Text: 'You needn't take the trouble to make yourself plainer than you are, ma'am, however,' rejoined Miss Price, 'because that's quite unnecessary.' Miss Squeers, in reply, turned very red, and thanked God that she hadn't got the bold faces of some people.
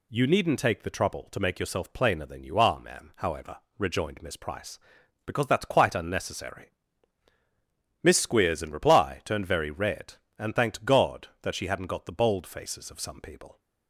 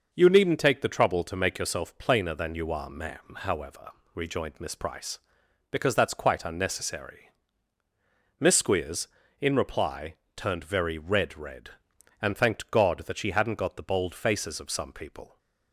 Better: first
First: none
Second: says "red" twice; at 11.3 s

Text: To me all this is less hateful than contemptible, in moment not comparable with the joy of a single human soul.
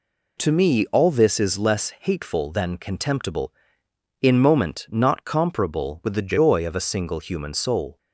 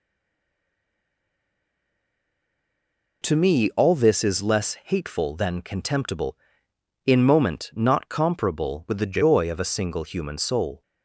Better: first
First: none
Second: stays silent before the first word; strong; until 3.2 s; 3.2 s long

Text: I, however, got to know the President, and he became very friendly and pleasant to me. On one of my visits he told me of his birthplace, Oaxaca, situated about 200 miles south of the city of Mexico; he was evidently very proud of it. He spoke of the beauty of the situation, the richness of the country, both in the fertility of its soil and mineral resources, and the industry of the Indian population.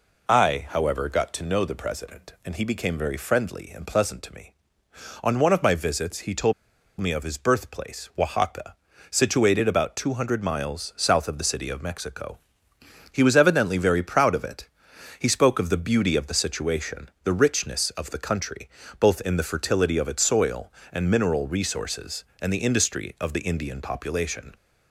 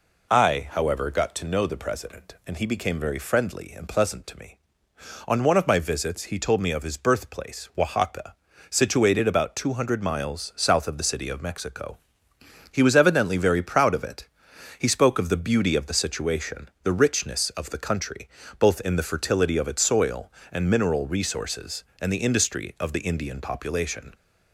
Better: second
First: pauses between "told" and "me"; noticeable; at 6.5 s; 0.47 s long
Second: none

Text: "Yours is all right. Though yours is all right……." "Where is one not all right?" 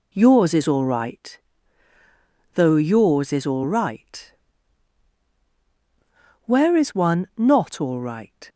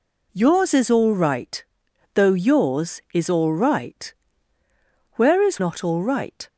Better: first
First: none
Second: skips "one"; at 5.5 s

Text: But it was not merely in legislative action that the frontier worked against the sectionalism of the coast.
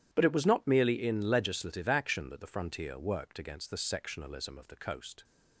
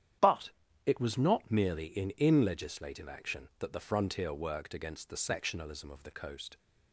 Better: first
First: starts louder than the rest; strong; until 1.1 s; 11 dB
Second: starts louder than the rest; strong; until 1.5 s; 10 dB // pauses between "But" and "it"; slight; at 0.4 s; 0.34 s long // says "in" twice; at 2.1 s

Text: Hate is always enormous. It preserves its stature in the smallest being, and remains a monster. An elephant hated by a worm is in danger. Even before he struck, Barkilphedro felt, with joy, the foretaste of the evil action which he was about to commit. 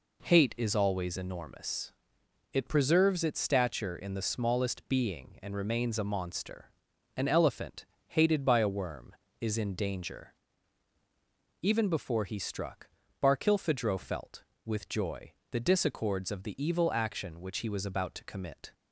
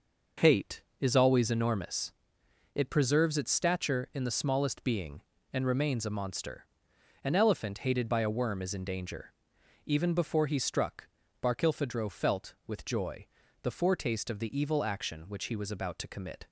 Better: second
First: pauses between "elephant" and "hated"; slight; at 7.8 s; 0.22 s long // says "disaccords" for "foretaste"; at 15.5 s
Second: none

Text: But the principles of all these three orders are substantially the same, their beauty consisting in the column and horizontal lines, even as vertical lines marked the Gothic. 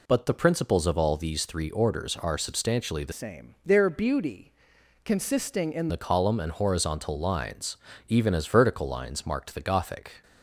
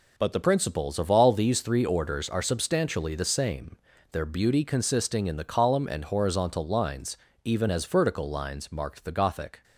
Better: second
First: changes voice from "same" to "in"; from 3.1 to 5.9 s; 2.8 s long // pauses between "beauty" and "consisting"; noticeable; at 4.5 s; 0.54 s long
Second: none

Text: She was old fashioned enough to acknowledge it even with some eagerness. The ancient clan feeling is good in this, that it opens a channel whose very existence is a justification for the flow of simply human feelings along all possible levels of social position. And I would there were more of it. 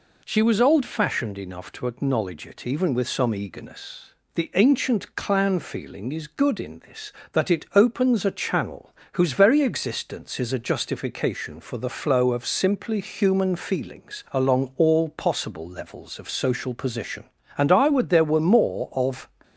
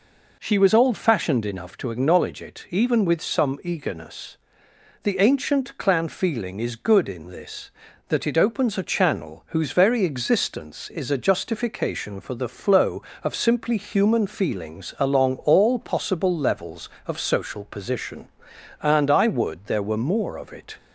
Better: second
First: pauses between "channel" and "whose"; slight; at 8.9 s; 0.18 s long // stops before "it"; at 19.4 s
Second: none

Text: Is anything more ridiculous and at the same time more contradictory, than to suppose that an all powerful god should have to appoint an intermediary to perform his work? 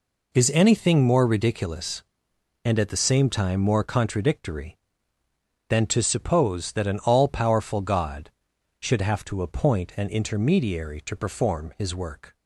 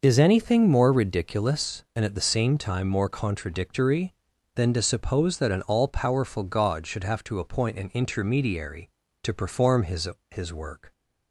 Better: first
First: none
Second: says "his" twice; at 10.3 s

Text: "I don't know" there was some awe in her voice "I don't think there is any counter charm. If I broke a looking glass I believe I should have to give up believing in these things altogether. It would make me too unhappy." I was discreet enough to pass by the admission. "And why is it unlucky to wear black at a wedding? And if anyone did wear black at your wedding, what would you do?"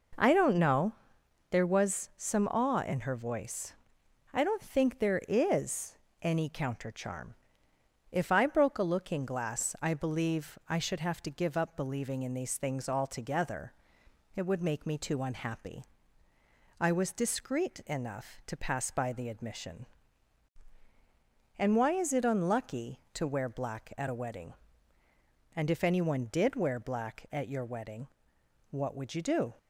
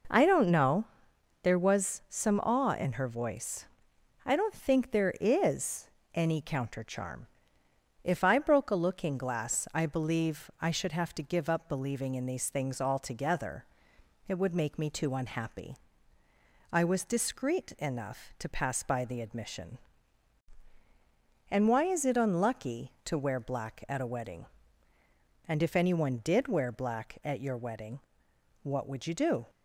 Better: neither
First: pauses between "know" and "there"; noticeable; at 0.9 s; 0.58 s long // pauses between "voice" and "I"; noticeable; at 3.7 s; 0.58 s long // pauses between "is" and "any"; slight; at 5.9 s; 0.26 s long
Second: pauses between "know" and "there"; noticeable; at 0.8 s; 0.58 s long // pauses between "voice" and "I"; noticeable; at 3.6 s; 0.58 s long // pauses between "is" and "any"; slight; at 5.8 s; 0.26 s long

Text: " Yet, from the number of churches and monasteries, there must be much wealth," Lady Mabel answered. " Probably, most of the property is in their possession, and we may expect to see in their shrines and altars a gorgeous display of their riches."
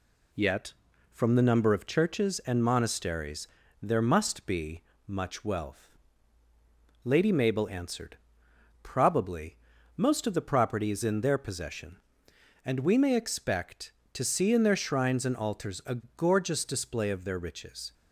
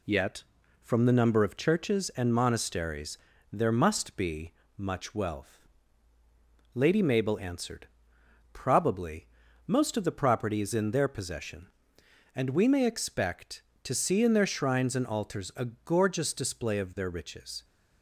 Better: neither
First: pauses between "be" and "much"; slight; at 4.8 s; 0.24 s long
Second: pauses between "be" and "much"; slight; at 4.5 s; 0.24 s long

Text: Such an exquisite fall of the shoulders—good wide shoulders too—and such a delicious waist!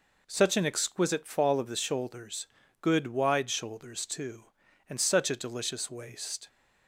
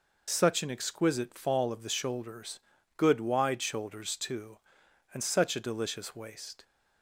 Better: first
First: none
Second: loses the start of "Such"; at 0.2 s; 70 ms

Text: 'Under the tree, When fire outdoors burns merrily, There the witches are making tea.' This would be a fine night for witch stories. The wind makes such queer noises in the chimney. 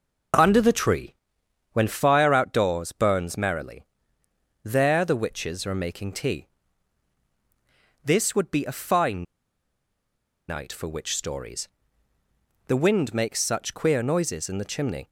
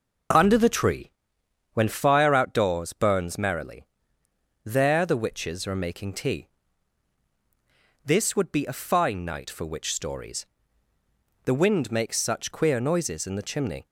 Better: second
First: pauses between "fine" and "night"; strong; at 9.2 s; 1.2 s long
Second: none

